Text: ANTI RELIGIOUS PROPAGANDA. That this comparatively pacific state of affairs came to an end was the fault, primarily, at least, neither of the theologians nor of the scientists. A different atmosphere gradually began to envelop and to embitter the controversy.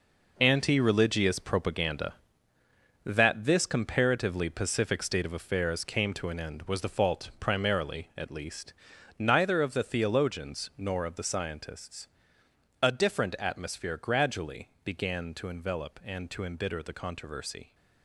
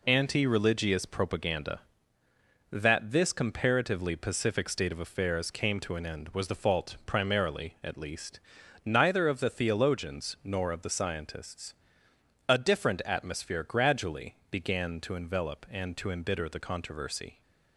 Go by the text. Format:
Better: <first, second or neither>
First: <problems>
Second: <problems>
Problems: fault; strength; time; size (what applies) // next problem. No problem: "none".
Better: second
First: gets quieter; strong; throughout; 10 dB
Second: none